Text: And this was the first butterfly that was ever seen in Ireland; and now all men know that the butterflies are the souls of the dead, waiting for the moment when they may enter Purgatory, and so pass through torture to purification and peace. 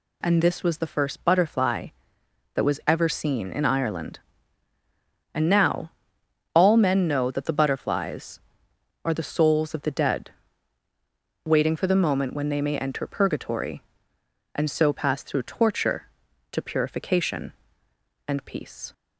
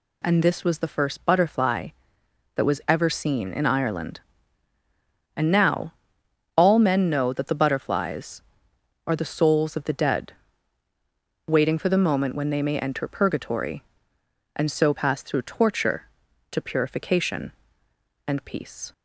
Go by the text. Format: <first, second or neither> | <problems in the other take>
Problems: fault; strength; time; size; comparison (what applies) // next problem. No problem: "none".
neither | pauses between "now" and "all"; noticeable; the same in both